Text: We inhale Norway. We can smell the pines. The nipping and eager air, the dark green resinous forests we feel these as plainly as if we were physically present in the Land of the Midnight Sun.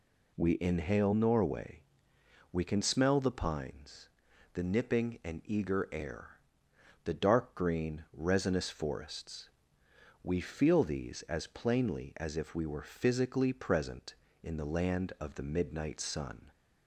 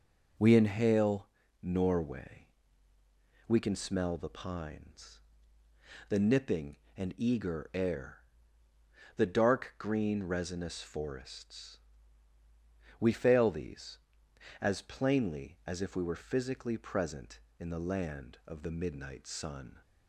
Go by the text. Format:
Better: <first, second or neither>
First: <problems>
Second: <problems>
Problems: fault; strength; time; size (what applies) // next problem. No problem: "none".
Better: first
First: pauses between "forests" and "we"; noticeable; at 9.4 s; 0.74 s long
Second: pauses between "inhale" and "Norway"; slight; at 1.2 s; 0.34 s long // pauses between "forests" and "we"; at 11.7 s; 1.2 s long // says "fail" for "feel"; at 13.1 s